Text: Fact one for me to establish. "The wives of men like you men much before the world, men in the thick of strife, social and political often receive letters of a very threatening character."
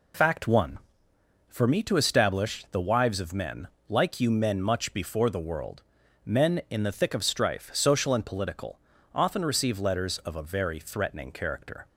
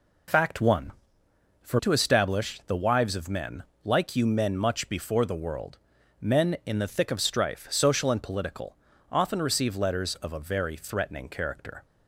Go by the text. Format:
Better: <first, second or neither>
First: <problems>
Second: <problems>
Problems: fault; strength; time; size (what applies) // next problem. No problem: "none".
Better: first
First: pauses between "men" and "like"; slight; at 3.6 s; 0.22 s long // pauses between "political" and "often"; slight; at 8.7 s; 0.34 s long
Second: skips "me"; at 1.7 s // pauses between "men" and "like"; slight; at 3.6 s; 0.22 s long // pauses between "political" and "often"; slight; at 8.7 s; 0.34 s long